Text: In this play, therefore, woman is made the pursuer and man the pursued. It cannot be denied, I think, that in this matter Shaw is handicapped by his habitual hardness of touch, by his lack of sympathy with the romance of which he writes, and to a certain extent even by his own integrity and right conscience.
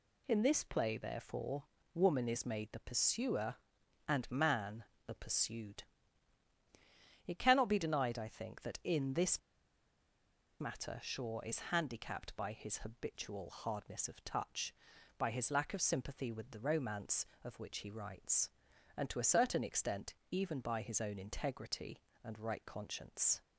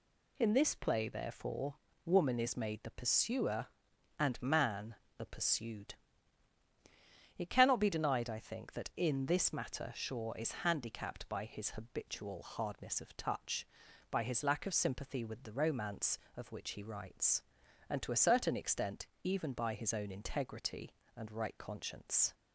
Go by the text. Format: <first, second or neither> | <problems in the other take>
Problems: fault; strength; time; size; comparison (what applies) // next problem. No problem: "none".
second | pauses between "man" and "the"; slight; at 4.8 s; 0.22 s long; slight in the second // pauses between "this" and "matter"; at 9.3 s; 1.2 s long // pauses between "extent" and "even"; slight; at 20.1 s; 0.16 s long; slight in the second